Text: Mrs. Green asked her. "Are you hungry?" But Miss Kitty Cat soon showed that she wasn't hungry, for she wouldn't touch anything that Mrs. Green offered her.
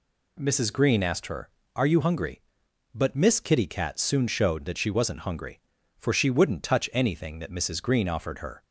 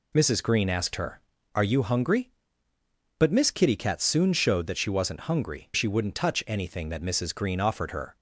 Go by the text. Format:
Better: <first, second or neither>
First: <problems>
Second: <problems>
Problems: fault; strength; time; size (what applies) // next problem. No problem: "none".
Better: first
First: none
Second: skips "for"; at 5.7 s